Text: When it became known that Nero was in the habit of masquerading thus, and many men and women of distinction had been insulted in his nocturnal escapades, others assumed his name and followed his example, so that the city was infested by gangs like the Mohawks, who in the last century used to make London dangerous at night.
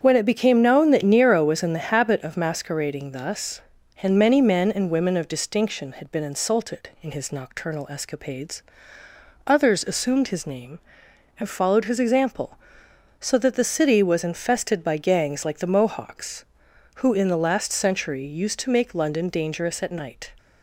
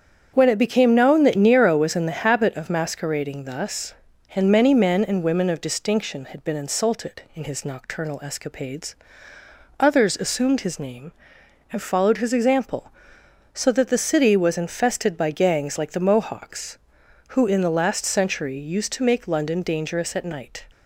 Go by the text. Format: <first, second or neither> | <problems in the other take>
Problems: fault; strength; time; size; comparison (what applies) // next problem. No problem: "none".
neither | starts louder than the rest; strong; the same in both